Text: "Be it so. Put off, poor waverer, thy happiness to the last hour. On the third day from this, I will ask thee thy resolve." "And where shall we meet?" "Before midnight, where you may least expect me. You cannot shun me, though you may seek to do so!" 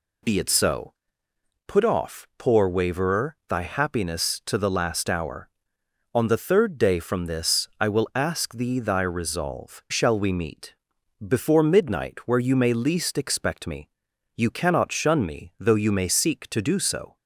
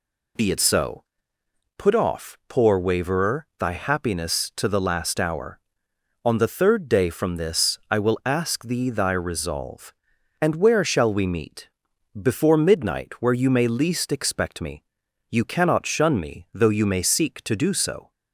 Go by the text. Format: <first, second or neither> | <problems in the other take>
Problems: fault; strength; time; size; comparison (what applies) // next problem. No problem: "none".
second | skips "And where"; at 9.8 s